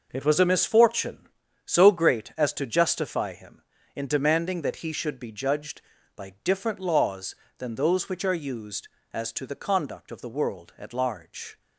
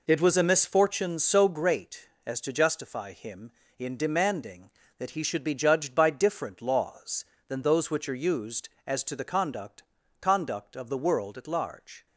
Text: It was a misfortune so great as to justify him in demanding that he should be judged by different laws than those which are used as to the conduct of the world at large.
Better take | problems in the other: first | says "conduct" twice; at 10.1 s

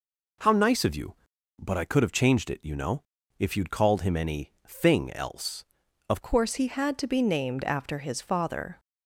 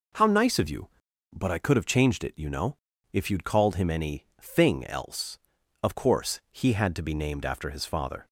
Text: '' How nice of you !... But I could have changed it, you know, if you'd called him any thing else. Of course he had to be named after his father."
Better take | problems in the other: second | changes voice at "course"; from 6.2 s on; 2.5 s long

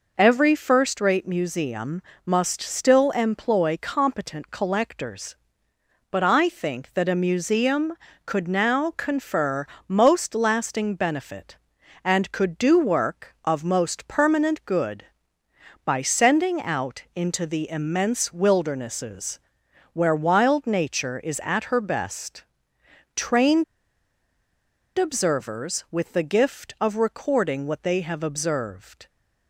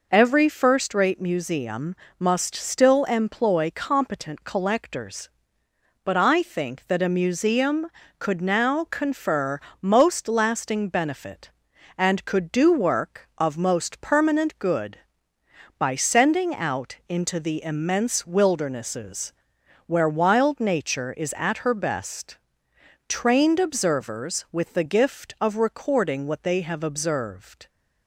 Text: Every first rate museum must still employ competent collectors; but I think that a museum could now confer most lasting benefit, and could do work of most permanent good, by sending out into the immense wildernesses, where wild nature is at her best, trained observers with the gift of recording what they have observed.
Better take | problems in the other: second | pauses between "museum" and "must"; slight; at 2.0 s; 0.24 s long; slight in the second // pauses between "confer" and "most"; slight; at 9.6 s; 0.24 s long; slight in the second // pauses between "trained" and "observers"; strong; at 23.6 s; 1.3 s long

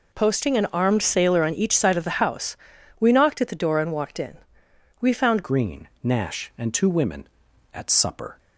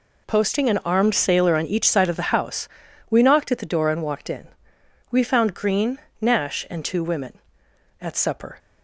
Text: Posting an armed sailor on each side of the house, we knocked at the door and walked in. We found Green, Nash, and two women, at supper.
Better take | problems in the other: second | changes voice at "Green"; from 5.4 s on; 2.9 s long

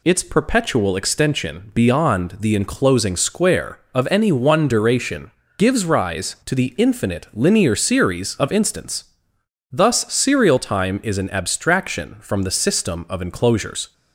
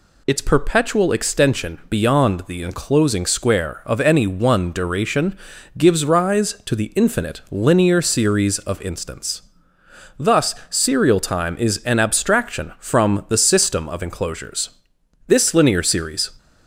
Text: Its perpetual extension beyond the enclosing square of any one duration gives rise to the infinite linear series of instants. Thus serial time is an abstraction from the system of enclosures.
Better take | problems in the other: first | pauses between "duration" and "gives"; at 5.3 s; 0.40 s long; slight in the first // goes on to say "This linear series"; noticeable; from 15.2 s on; 1.0 s long

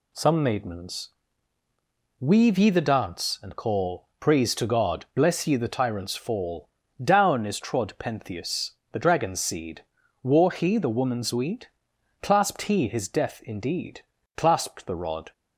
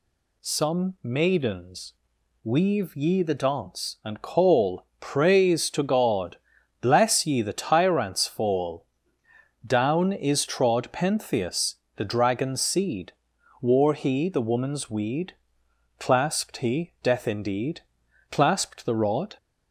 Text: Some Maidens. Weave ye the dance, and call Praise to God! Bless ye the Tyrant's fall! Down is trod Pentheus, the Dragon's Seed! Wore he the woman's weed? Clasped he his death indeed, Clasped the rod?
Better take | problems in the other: first | pauses between "call" and "Praise"; slight; at 4.8 s; 0.16 s long // skips "his"; at 16.9 s

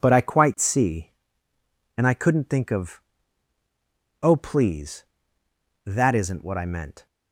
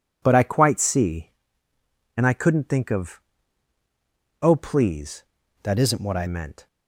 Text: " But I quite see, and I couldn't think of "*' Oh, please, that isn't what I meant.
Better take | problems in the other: first | changes voice from "that" to "I"; from 5.6 to 6.2 s; 0.6 s long

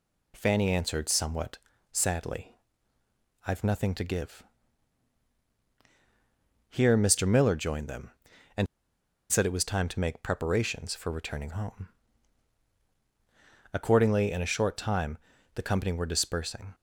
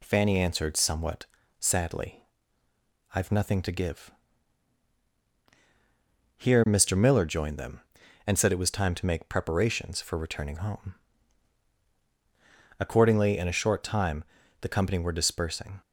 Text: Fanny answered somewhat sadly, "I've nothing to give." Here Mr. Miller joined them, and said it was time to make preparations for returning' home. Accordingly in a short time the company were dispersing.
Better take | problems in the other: second | pauses between "somewhat" and "sadly"; slight; at 1.5 s; 0.36 s long; slight in the second // pauses between "and" and "said"; noticeable; at 8.6 s; 0.64 s long // pauses between "time" and "the"; slight; at 15.1 s; 0.36 s long; slight in the second

